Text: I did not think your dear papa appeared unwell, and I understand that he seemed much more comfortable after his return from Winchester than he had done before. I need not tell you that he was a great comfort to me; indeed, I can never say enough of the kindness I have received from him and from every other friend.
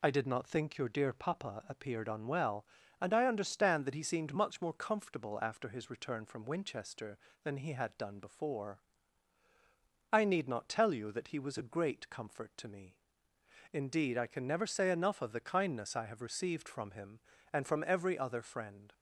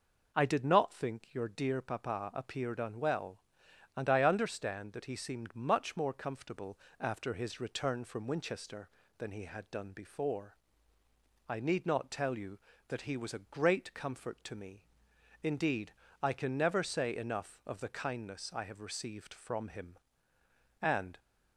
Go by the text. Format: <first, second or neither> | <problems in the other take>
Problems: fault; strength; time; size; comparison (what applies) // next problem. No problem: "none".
first | pauses between "comfortable" and "after"; slight; at 6.7 s; 0.22 s long // stops before "from every other friend"; at 21.1 s